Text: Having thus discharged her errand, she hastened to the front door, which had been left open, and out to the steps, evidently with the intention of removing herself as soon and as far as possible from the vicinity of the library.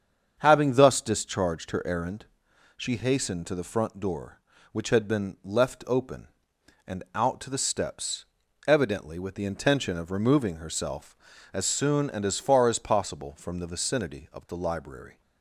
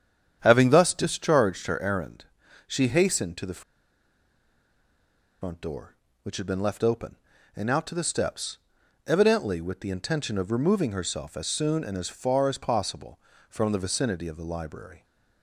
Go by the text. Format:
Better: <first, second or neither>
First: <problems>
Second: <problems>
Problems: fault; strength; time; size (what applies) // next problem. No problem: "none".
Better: first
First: starts louder than the rest; strong; until 1.3 s; 7.5 dB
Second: starts louder than the rest; strong; until 1.4 s; 9 dB // pauses between "the" and "front"; strong; at 3.6 s; 1.8 s long